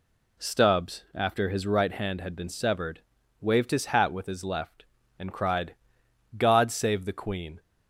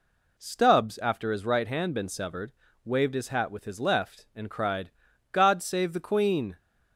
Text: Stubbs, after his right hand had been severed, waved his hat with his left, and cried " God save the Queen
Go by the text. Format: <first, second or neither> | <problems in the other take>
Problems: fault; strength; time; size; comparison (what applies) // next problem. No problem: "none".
first | skips "had"; at 1.9 s